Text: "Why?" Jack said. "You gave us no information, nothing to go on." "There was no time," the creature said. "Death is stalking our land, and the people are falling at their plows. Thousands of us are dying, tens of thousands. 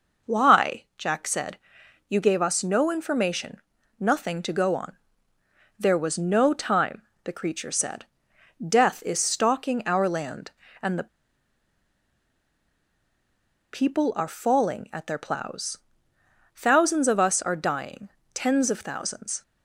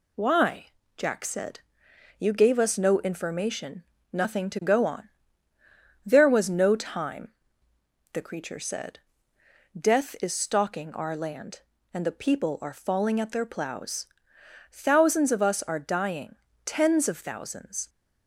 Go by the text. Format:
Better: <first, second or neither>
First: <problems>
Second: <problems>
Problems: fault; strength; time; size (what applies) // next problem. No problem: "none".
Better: second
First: pauses between "the" and "people"; strong; at 11.0 s; 2.6 s long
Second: none